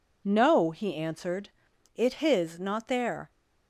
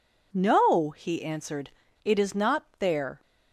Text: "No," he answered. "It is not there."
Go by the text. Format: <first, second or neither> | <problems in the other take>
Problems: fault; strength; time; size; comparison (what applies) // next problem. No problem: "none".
second | says "his" for "is"; at 2.1 s